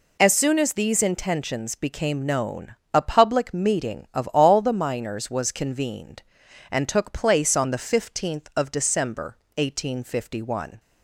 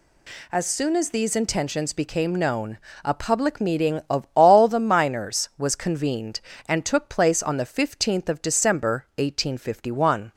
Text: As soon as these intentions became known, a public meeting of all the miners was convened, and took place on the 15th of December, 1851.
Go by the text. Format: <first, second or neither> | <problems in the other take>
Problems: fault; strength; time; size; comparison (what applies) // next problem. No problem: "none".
neither | none